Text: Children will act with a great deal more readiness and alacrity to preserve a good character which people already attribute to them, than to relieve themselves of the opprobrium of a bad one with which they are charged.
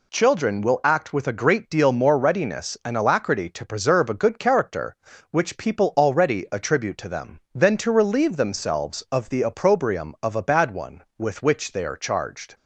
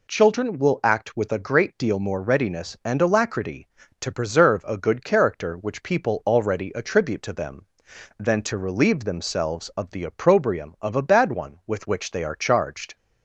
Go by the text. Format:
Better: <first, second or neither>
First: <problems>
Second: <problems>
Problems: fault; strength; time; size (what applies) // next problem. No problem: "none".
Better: neither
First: none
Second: none